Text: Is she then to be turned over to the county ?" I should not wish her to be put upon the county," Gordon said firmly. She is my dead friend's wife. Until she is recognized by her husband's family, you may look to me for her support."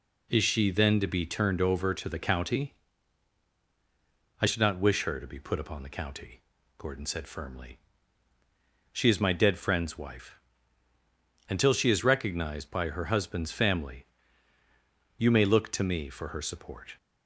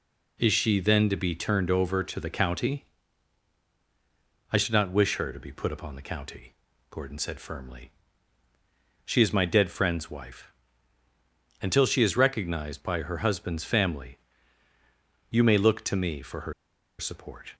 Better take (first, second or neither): first